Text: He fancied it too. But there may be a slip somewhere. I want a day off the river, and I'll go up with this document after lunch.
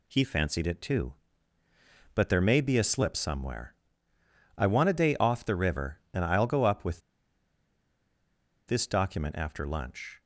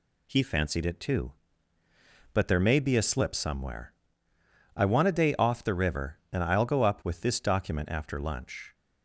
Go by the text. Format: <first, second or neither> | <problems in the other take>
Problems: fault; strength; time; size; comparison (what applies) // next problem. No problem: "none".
second | pauses between "with" and "this"; strong; at 6.9 s; 1.6 s long